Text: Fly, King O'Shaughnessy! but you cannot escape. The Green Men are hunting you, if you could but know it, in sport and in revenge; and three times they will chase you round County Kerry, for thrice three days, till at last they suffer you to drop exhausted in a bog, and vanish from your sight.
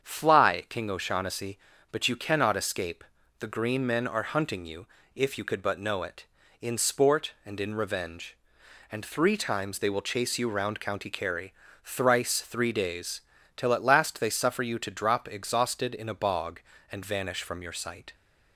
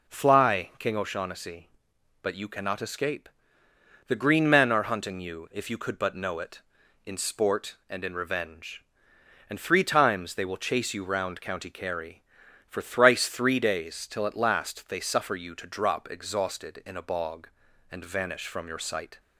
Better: second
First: starts louder than the rest; strong; until 1.0 s; 7.5 dB // skips "for"; at 11.6 s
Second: none

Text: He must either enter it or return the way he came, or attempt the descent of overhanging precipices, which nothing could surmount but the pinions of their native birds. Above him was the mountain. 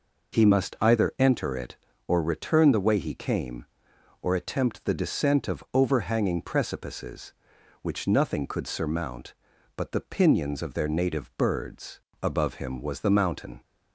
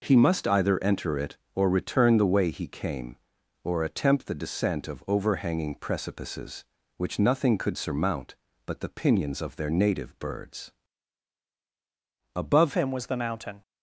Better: first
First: none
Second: changes voice at "him"; from 12.7 s on; 0.9 s long

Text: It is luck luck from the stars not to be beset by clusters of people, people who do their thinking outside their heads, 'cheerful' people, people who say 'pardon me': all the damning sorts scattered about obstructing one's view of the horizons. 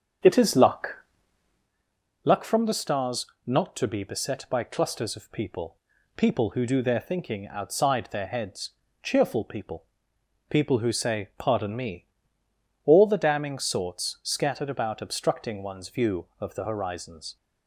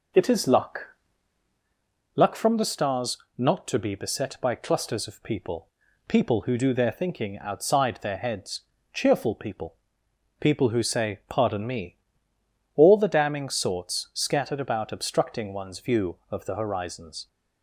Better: second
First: starts louder than the rest; strong; until 1.7 s; 7 dB // pauses between "luck" and "luck"; strong; at 0.9 s; 1.2 s long // pauses between "stars" and "not"; slight; at 3.2 s; 0.18 s long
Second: pauses between "luck" and "luck"; strong; at 0.8 s; 1.2 s long // pauses between "stars" and "not"; slight; at 3.1 s; 0.18 s long

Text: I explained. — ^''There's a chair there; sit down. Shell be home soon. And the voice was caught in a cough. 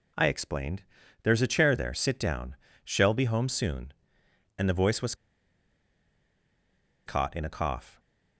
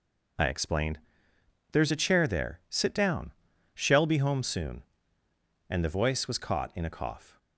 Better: second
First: pauses between "was" and "caught"; strong; at 5.1 s; 1.9 s long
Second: none

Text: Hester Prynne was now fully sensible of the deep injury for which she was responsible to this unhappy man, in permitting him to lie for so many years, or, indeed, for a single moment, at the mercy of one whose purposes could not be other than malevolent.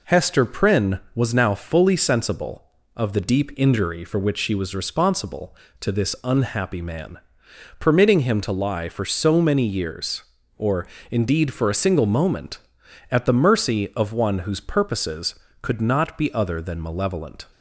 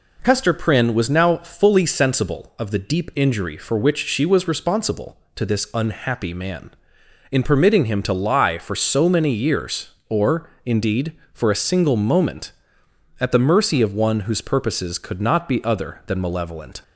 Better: second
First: skips "in"; at 7.4 s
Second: none

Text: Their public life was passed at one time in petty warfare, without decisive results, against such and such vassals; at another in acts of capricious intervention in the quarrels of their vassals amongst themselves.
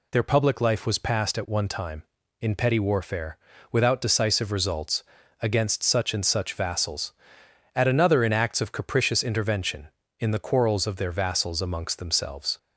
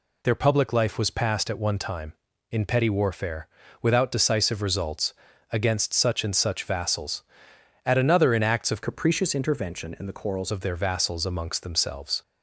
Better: first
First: none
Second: changes voice from "capricious" to "quarrels"; from 8.8 to 10.5 s; 1.7 s long

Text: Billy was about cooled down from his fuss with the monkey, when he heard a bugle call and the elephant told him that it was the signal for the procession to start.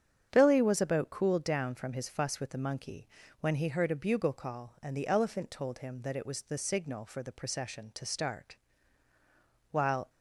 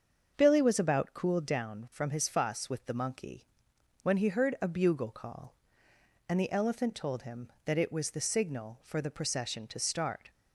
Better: second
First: starts louder than the rest; strong; until 1.3 s; 8 dB // goes on to say "While"; slight; from 9.7 s on; 0.38 s long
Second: starts louder than the rest; until 1.3 s; 6.5 dB

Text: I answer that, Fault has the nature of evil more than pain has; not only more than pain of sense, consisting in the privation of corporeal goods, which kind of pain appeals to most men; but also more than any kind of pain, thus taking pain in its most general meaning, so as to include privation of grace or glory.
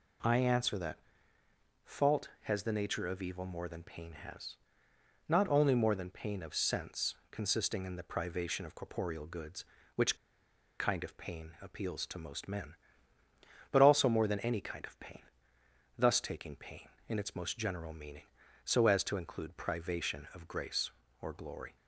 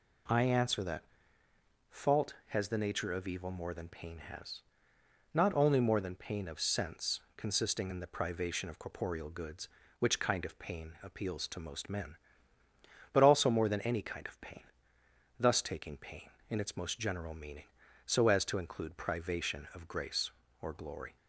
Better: second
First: pauses between "which" and "kind"; noticeable; at 10.1 s; 0.64 s long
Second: none

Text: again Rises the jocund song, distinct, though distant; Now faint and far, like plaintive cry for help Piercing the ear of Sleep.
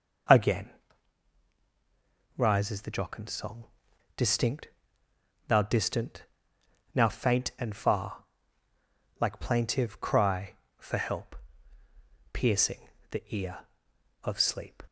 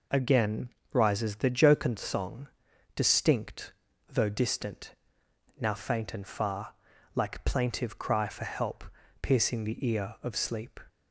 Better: second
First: pauses between "again" and "Rises"; strong; at 0.7 s; 1.6 s long // says "thou" for "though"; at 5.4 s // pauses between "help" and "Piercing"; noticeable; at 11.3 s; 0.96 s long // pauses between "Piercing" and "the"; slight; at 12.8 s; 0.22 s long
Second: pauses between "again" and "Rises"; slight; at 0.6 s; 0.22 s long // pauses between "help" and "Piercing"; slight; at 8.8 s; 0.36 s long

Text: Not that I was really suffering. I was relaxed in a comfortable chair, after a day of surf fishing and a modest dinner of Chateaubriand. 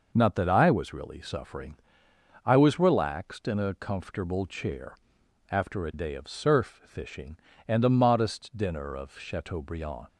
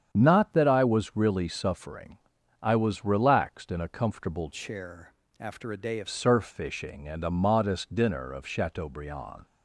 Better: first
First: none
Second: starts louder than the rest; strong; until 1.1 s; 8 dB // changes voice from "chair" to "of"; from 4.5 to 6.0 s; 1.5 s long

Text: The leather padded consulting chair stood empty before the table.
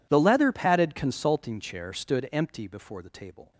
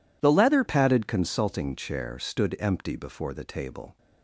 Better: first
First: none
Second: changes voice at "padded"; from 0.6 s on; 3.3 s long

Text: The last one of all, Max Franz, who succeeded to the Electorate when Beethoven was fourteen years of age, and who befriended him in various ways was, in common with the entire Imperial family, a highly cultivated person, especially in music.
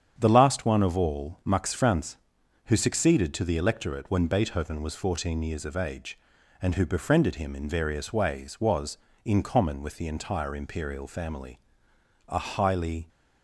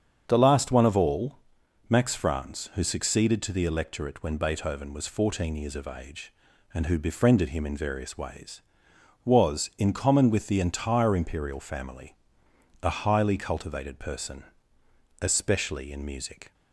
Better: second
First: starts louder than the rest; strong; until 1.1 s; 8.5 dB // stops before "cultivated person especially in music"; at 13.0 s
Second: starts louder than the rest; strong; until 1.2 s; 7.5 dB

